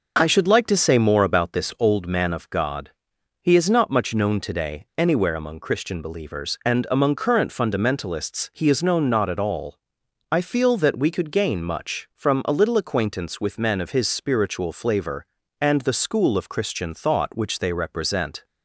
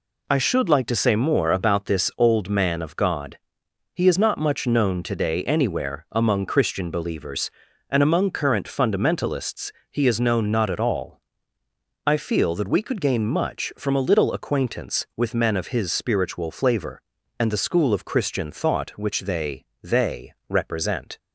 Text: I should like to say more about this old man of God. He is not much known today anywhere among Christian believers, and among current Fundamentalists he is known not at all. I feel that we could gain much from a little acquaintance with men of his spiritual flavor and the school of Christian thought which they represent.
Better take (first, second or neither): first